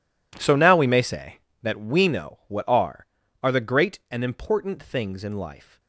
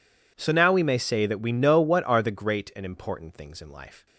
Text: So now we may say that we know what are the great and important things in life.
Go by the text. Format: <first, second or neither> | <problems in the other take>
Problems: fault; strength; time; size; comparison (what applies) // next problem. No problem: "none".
second | says "are" twice; at 3.4 s